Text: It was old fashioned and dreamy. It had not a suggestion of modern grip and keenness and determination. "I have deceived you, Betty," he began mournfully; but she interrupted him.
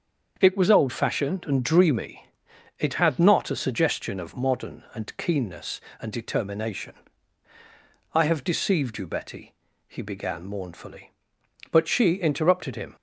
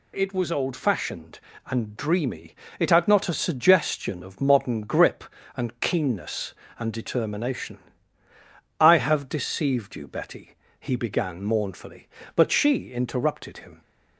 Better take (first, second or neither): second